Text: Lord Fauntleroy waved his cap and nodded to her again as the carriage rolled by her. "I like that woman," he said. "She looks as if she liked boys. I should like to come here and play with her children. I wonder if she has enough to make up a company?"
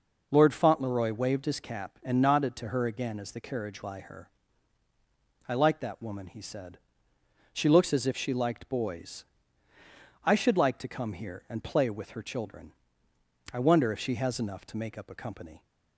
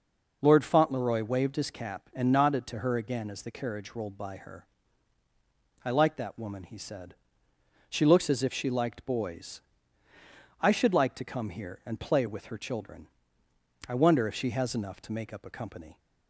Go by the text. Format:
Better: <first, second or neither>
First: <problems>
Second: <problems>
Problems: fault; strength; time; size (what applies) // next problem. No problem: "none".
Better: second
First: skips "rolled"; at 3.8 s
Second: none